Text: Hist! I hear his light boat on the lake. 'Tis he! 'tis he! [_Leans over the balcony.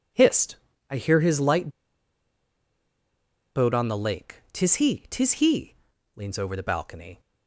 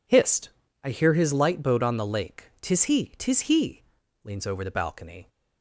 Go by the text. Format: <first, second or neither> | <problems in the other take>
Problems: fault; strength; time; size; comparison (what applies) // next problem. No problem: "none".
second | pauses between "light" and "boat"; strong; at 1.6 s; 1.8 s long